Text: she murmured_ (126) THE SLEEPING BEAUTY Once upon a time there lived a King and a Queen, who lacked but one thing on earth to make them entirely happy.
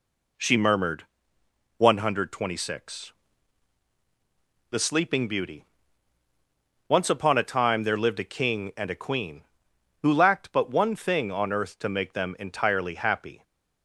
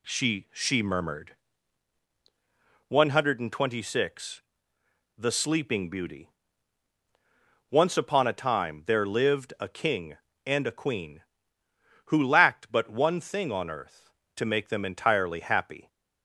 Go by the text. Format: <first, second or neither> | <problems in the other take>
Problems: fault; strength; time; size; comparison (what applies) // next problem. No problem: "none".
first | says "she" twice; at 0.5 s // pauses between "BEAUTY" and "Once"; strong; at 6.2 s; 1.4 s long; also in the first